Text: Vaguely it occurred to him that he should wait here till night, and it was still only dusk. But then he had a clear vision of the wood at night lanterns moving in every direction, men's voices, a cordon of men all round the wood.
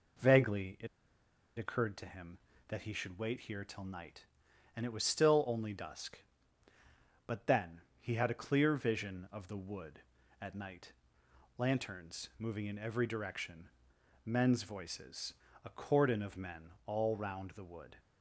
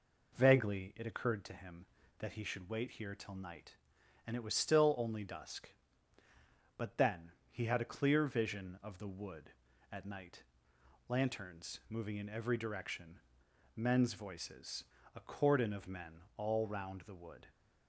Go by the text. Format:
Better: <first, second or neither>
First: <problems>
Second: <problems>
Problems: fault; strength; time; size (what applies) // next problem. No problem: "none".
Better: second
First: pauses between "it" and "occurred"; noticeable; at 0.8 s; 0.70 s long // pauses between "then" and "he"; slight; at 7.8 s; 0.20 s long // pauses between "night" and "lanterns"; noticeable; at 10.9 s; 0.66 s long // pauses between "men" and "all"; slight; at 16.7 s; 0.16 s long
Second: pauses between "then" and "he"; slight; at 7.3 s; 0.20 s long // pauses between "night" and "lanterns"; noticeable; at 10.4 s; 0.66 s long // pauses between "men" and "all"; slight; at 16.2 s; 0.16 s long